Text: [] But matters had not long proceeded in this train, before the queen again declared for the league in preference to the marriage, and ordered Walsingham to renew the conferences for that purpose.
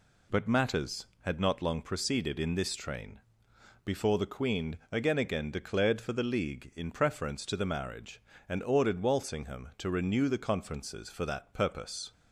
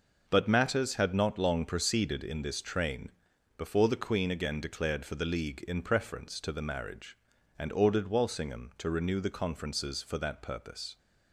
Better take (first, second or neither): second